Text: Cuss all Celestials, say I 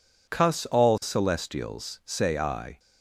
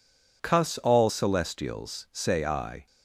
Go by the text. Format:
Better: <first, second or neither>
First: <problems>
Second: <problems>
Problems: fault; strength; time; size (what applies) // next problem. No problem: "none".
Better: neither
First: none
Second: none